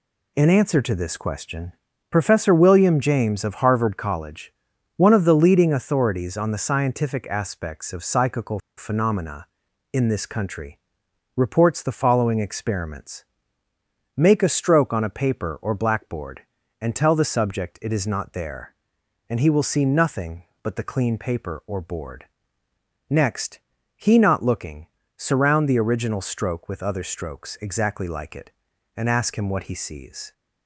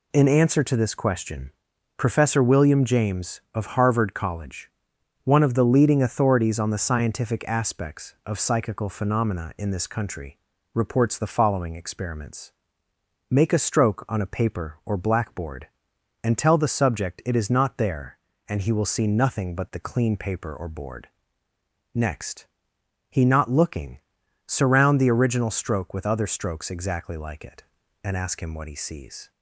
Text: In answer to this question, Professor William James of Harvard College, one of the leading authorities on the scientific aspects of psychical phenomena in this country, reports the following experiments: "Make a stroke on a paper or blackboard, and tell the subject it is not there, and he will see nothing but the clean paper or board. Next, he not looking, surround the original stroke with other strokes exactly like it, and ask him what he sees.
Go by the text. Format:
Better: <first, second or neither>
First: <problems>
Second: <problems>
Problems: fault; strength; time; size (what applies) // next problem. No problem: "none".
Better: second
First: pauses between "psychical" and "phenomena"; slight; at 8.5 s; 0.19 s long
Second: none